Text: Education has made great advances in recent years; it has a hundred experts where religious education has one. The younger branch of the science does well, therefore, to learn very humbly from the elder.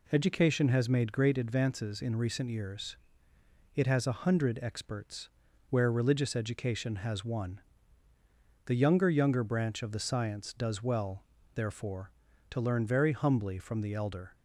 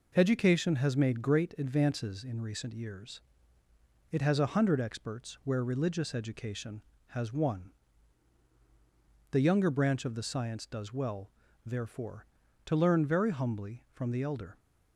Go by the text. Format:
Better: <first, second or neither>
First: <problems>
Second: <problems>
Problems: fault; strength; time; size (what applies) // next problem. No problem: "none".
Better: second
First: pauses between "experts" and "where"; at 5.2 s; 0.42 s long // says "younger" twice; at 9.0 s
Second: none